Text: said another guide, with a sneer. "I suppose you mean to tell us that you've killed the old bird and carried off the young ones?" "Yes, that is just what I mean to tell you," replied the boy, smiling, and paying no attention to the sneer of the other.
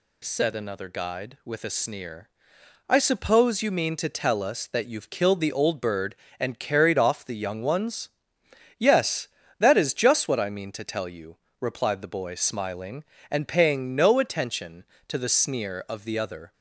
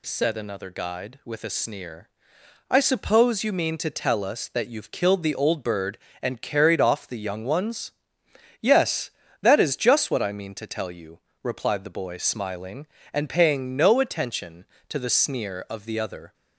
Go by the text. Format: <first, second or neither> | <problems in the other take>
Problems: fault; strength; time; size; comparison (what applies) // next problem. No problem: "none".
neither | none